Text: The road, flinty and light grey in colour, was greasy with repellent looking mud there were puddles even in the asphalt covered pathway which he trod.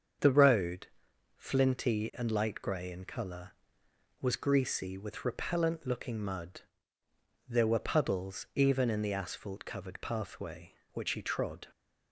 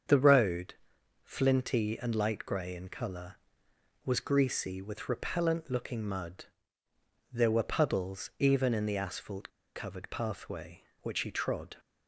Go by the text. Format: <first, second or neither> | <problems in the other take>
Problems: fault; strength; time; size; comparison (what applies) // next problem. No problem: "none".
first | starts louder than the rest; until 1.5 s; 7 dB; also in the first // pauses between "mud" and "there"; noticeable; at 6.4 s; 0.88 s long; noticeable in the first // pauses between "asphalt" and "covered"; slight; at 9.4 s; 0.27 s long